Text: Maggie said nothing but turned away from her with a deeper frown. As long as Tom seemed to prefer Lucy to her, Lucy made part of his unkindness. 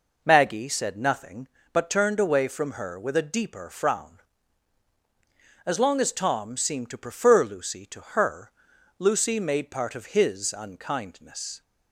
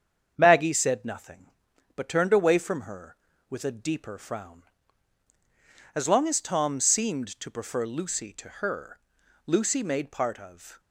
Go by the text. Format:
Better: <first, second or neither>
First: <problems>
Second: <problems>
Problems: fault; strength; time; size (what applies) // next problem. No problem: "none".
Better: first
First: none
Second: starts louder than the rest; strong; until 1.3 s; 7.5 dB // stops before "his unkindness"; at 10.7 s